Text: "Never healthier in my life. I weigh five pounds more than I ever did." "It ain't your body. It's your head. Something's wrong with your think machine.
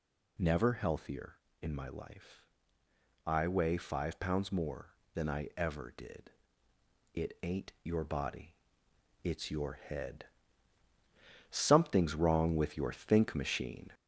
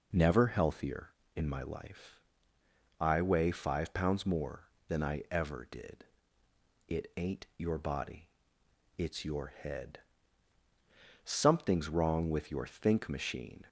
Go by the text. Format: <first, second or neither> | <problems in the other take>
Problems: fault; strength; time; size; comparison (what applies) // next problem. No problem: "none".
second | gets louder; slight; throughout; 3 dB